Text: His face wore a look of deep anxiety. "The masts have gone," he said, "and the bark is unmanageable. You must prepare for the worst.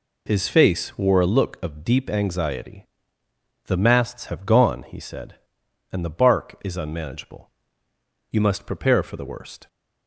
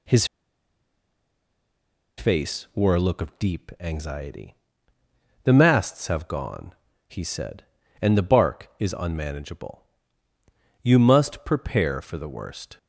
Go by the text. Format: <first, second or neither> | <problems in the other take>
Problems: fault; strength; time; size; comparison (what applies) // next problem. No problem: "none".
first | pauses between "His" and "face"; strong; at 0.2 s; 1.9 s long